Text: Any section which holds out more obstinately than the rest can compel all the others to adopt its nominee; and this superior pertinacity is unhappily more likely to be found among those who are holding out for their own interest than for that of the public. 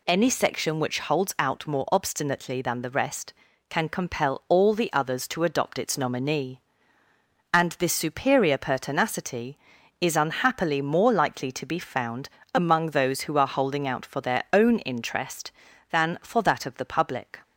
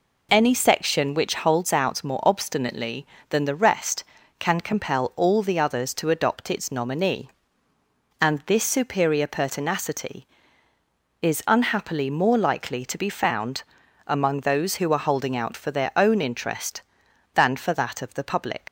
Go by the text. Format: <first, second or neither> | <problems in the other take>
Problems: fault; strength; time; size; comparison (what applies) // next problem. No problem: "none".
first | pauses between "found" and "among"; at 13.6 s; 0.42 s long; slight in the first // leaves "public" unfinished; at 18.6 s; 70 ms